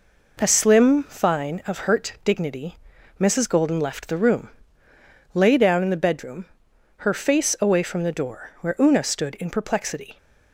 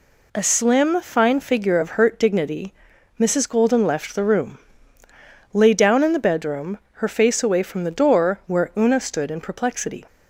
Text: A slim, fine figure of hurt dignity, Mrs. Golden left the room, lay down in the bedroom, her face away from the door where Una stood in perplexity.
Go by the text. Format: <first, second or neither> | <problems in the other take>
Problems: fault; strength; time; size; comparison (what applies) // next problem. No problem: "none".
second | skips "figure"; at 1.6 s